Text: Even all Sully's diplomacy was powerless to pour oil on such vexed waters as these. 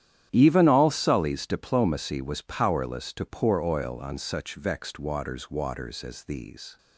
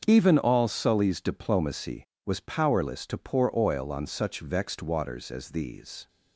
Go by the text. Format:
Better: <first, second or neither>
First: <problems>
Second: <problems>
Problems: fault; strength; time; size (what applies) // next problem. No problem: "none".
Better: second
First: starts louder than the rest; strong; until 1.3 s; 10.5 dB // says "waters" twice; at 5.4 s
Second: starts louder than the rest; until 1.0 s; 7 dB